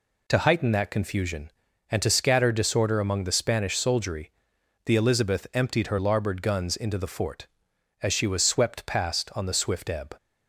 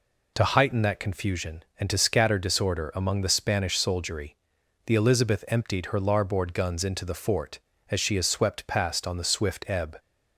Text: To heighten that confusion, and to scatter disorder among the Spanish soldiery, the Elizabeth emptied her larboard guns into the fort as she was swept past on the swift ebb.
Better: first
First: none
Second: says "is" for "was"; at 8.1 s

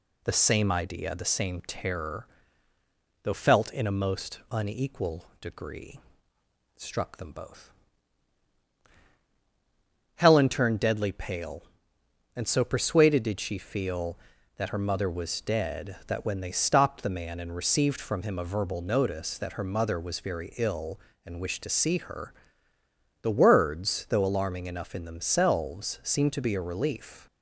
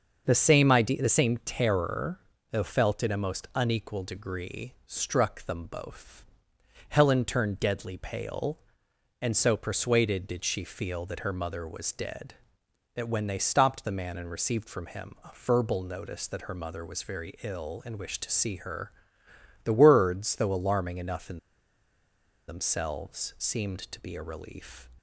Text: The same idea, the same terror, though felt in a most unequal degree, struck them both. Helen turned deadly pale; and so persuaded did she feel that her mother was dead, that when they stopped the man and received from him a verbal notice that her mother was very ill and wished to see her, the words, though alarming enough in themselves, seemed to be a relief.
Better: first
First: none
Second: starts louder than the rest; until 1.2 s; 6.5 dB // pauses between "in" and "themselves"; at 21.3 s; 1.0 s long

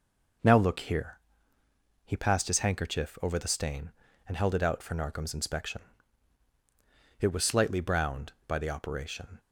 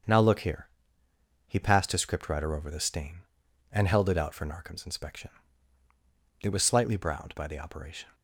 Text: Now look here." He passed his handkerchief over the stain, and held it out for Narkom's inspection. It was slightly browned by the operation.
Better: first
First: none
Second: starts louder than the rest; until 1.8 s; 7 dB // says "scriptwriter" for "handkerchief"; at 2.0 s

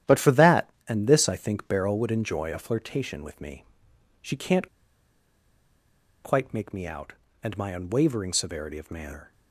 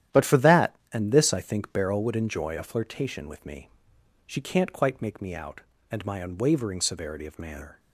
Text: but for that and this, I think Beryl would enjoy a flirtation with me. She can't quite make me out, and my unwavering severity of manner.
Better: second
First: starts louder than the rest; strong; until 1.2 s; 11 dB // pauses between "can't" and "quite"; strong; at 4.6 s; 1.5 s long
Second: starts louder than the rest; strong; until 1.3 s; 11 dB

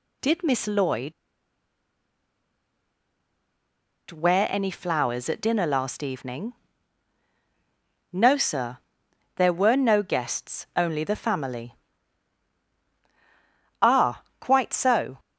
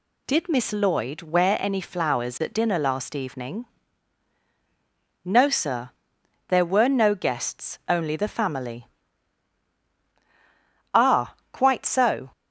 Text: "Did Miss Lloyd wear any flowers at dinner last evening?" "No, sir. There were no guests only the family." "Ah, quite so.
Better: second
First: pauses between "Lloyd" and "wear"; strong; at 1.1 s; 2.9 s long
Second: none

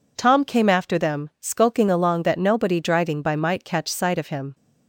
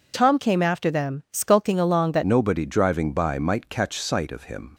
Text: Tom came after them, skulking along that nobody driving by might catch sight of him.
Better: first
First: none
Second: changes voice at "nobody"; from 2.2 s on; 2.5 s long

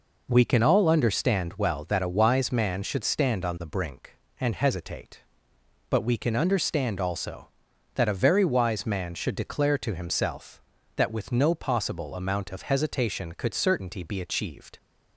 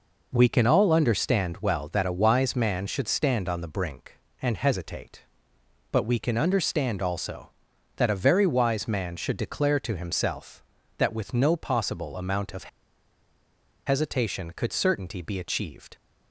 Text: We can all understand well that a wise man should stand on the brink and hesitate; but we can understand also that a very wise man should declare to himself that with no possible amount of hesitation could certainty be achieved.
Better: first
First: none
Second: pauses between "of" and "hesitation"; at 12.6 s; 1.1 s long

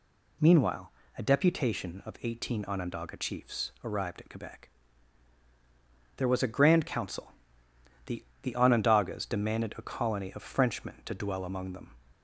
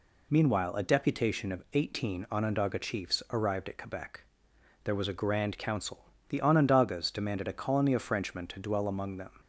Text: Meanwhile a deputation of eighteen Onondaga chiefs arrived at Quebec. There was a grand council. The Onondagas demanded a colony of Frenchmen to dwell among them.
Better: second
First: pauses between "Meanwhile" and "a"; slight; at 0.9 s; 0.24 s long // says "The" twice; at 8.4 s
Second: none

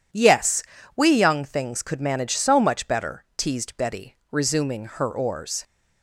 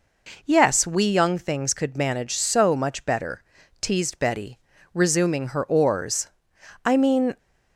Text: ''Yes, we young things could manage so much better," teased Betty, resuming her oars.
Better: first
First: none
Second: goes on to say "I mean"; from 6.8 s on; 0.54 s long

